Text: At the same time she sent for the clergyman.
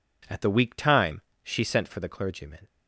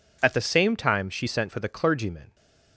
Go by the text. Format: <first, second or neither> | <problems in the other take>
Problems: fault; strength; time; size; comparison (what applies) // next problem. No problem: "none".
second | says "weak" for "same"; at 0.5 s // pauses between "time" and "she"; slight; at 1.2 s; 0.22 s long